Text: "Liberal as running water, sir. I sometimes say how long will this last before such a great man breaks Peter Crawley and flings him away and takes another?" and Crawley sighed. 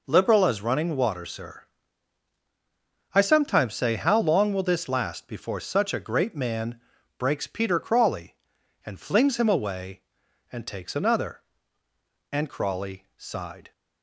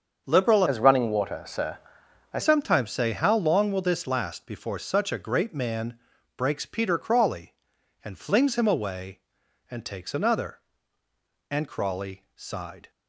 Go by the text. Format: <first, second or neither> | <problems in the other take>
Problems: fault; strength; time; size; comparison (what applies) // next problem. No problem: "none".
first | starts louder than the rest; until 1.2 s; 7 dB // changes voice from "as" to "I"; from 0.6 to 2.3 s; 1.7 s long // pauses between "man" and "breaks"; at 5.9 s; 0.38 s long; also in the first